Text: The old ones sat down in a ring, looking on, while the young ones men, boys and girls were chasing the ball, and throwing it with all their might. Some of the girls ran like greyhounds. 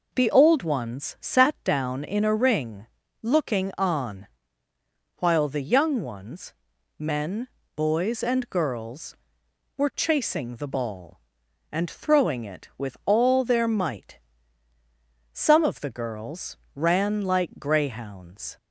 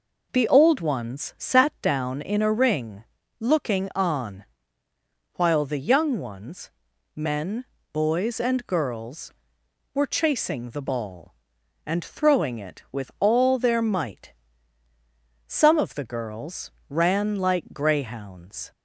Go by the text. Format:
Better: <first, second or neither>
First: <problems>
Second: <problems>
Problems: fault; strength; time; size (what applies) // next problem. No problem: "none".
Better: neither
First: pauses between "ones" and "men"; noticeable; at 6.5 s; 0.46 s long // pauses between "girls" and "ran"; slight; at 16.5 s; 0.22 s long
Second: pauses between "ones" and "men"; noticeable; at 6.6 s; 0.46 s long // pauses between "girls" and "ran"; slight; at 16.6 s; 0.22 s long